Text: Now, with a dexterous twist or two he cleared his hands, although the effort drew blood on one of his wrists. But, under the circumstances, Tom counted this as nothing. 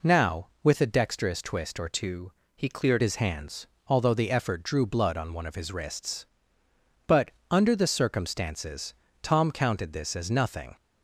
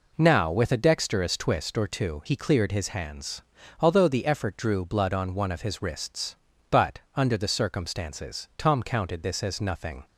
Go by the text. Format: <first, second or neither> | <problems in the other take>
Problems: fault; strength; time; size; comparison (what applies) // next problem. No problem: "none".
second | changes voice from "two" to "cleared"; from 1.9 to 3.0 s; 1.1 s long // pauses between "two" and "he"; slight; at 2.3 s; 0.24 s long